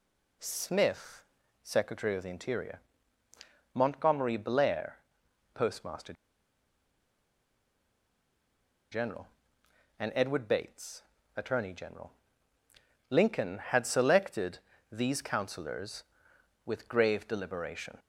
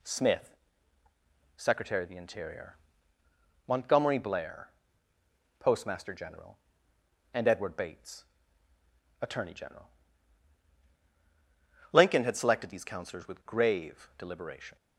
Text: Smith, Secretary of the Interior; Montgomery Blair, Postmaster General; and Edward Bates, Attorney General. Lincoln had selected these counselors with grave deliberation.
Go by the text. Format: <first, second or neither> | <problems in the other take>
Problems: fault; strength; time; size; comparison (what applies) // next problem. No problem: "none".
second | pauses between "Postmaster" and "General"; strong; at 6.1 s; 2.7 s long // pauses between "selected" and "these"; slight; at 14.5 s; 0.32 s long